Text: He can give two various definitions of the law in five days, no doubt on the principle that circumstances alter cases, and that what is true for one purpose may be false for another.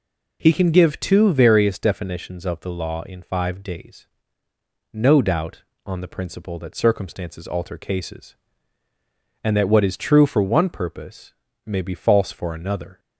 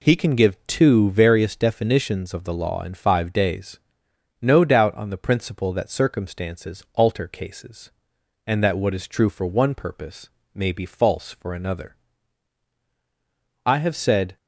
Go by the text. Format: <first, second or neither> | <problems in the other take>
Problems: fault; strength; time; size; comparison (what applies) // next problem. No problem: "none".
first | pauses between "purpose" and "may"; slight; at 10.3 s; 0.24 s long; slight in the first // goes on to say "I have said"; noticeable; from 13.6 s on; 0.70 s long